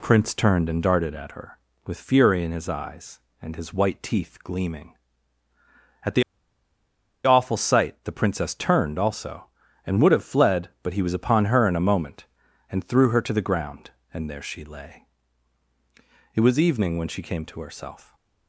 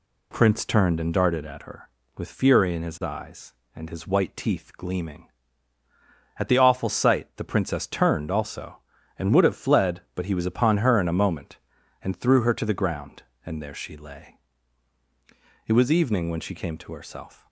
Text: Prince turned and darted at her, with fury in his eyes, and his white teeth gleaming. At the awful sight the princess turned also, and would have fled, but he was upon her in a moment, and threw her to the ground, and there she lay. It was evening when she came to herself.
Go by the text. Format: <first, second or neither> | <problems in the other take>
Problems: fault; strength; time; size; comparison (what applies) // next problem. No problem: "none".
second | pauses between "the" and "awful"; at 6.2 s; 1.0 s long